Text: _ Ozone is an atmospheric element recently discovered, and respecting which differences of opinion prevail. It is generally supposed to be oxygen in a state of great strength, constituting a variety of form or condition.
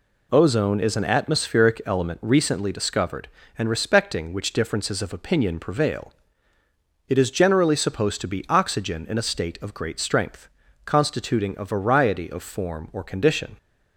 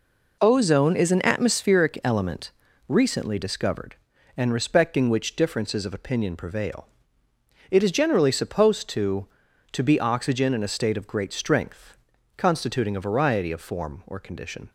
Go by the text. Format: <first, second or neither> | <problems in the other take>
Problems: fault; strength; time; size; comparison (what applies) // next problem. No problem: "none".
first | pauses between "element" and "recently"; slight; at 2.5 s; 0.34 s long // says "to" twice; at 9.7 s